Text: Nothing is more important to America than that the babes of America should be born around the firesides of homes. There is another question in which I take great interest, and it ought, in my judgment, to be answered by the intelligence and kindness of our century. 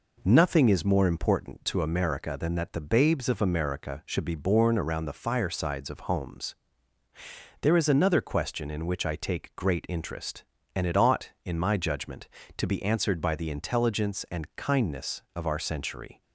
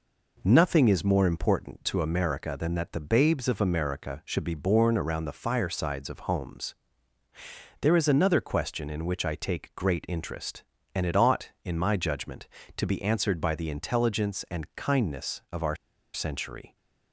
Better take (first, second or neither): first